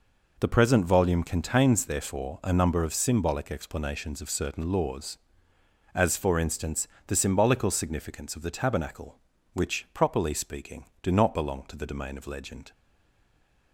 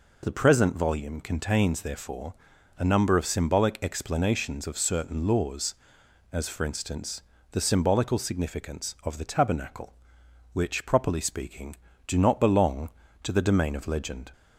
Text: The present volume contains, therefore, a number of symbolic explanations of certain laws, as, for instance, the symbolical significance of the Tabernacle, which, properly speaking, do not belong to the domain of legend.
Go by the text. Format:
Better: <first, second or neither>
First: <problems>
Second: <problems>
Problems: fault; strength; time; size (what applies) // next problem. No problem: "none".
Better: second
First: stays silent after the last word; from 12.7 s on; 1.0 s long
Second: none